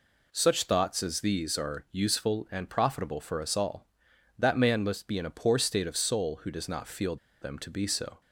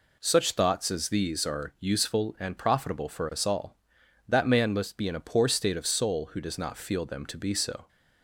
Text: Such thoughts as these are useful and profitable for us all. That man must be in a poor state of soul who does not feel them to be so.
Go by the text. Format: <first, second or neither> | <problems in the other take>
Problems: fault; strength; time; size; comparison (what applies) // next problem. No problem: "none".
second | pauses between "feel" and "them"; slight; at 7.1 s; 0.25 s long